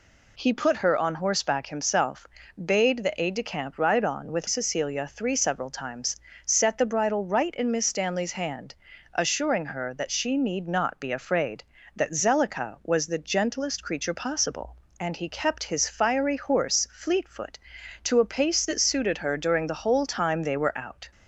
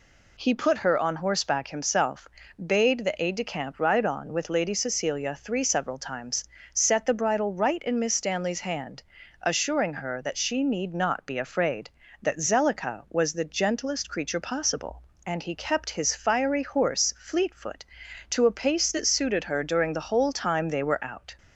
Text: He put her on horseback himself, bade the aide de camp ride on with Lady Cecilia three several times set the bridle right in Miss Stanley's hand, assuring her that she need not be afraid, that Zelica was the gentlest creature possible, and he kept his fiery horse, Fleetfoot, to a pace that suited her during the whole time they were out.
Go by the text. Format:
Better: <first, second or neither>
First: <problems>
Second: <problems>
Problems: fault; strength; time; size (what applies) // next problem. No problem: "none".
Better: second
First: skips "Lady"; at 4.4 s // pauses between "times" and "set"; slight; at 6.1 s; 0.30 s long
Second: pauses between "times" and "set"; slight; at 6.4 s; 0.30 s long